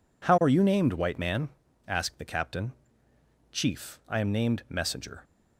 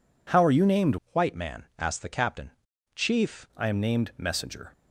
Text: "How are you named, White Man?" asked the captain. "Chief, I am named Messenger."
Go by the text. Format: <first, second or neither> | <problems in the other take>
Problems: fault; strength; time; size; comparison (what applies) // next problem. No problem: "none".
first | changes voice from "White" to "Chief"; from 1.1 to 3.4 s; 2.3 s long